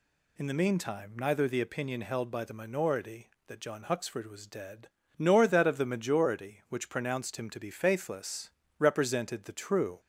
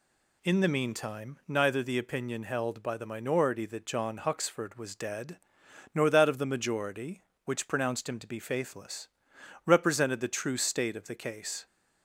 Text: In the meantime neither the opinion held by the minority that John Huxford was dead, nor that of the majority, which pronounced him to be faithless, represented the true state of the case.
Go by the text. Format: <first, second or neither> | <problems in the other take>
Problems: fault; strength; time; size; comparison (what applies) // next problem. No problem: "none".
second | stops before "state of the case"; at 9.9 s